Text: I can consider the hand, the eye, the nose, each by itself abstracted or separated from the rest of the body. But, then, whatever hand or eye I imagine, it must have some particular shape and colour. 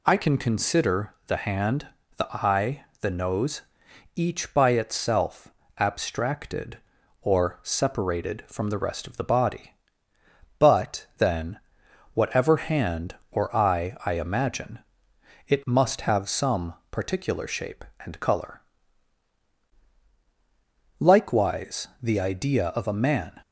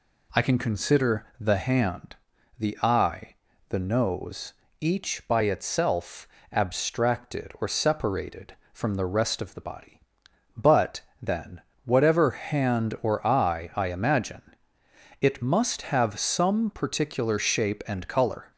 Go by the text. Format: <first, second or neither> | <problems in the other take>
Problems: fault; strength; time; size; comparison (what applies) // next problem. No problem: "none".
second | pauses between "itself" and "abstracted"; slight; at 5.5 s; 0.24 s long; slight in the second // pauses between "some" and "particular"; slight; at 16.7 s; 0.18 s long // goes on to say "Likewise the idea of a man"; strong; from 20.9 s on; 2.4 s long